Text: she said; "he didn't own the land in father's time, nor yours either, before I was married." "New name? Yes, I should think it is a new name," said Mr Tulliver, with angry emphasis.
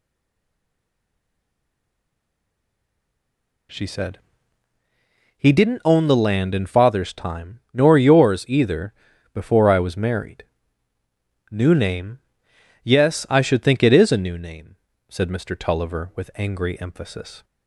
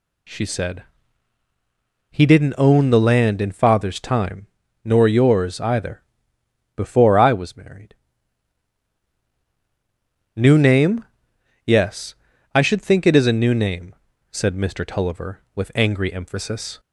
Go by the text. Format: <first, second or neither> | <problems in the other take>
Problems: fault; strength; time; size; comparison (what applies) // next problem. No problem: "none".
second | stays silent before the first word; strong; until 3.7 s; 3.7 s long